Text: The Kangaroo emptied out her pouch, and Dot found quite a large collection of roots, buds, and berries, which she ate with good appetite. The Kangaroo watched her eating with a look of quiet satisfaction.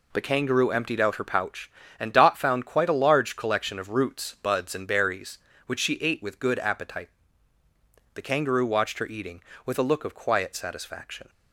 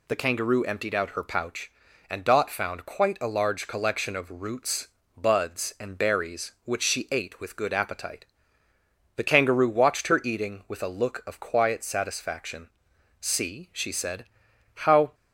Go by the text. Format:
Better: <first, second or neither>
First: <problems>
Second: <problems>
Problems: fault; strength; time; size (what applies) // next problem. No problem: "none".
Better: first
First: none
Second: goes on to say "See she said how"; strong; from 13.1 s on; 1.9 s long